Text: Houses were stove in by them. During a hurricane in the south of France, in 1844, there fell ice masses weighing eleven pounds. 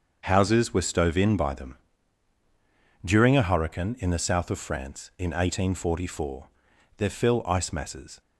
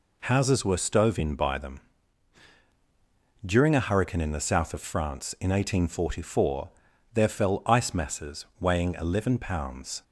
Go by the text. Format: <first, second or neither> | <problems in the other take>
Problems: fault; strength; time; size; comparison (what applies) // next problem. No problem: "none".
second | starts louder than the rest; until 1.2 s; 6.5 dB // stops before "weighing eleven pounds"; at 8.2 s